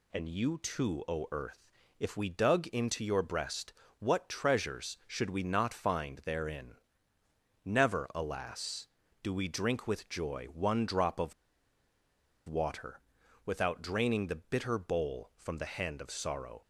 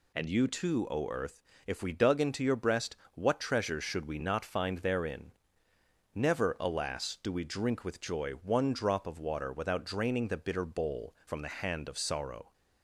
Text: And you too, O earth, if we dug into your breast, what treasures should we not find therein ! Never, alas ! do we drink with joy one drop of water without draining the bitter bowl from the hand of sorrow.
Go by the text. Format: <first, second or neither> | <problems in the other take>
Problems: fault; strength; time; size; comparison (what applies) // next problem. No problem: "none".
second | pauses between "of" and "water"; at 11.3 s; 1.1 s long // pauses between "water" and "without"; noticeable; at 12.9 s; 0.46 s long